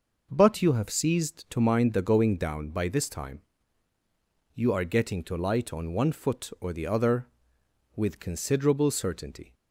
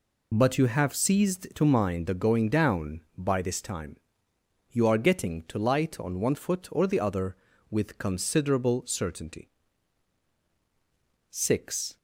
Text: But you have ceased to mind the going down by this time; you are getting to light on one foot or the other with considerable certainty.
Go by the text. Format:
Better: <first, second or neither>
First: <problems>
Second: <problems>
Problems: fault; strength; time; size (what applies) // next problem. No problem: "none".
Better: first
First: none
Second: goes on to say "Six"; noticeable; from 11.2 s on; 0.68 s long